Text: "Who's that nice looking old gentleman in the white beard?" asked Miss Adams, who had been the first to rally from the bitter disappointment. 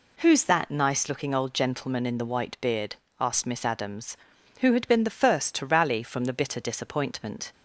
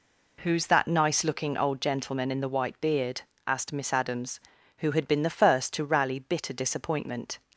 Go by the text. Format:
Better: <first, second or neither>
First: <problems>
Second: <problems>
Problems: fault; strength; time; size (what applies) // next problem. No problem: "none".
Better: first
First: none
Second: skips "from the"; at 6.1 s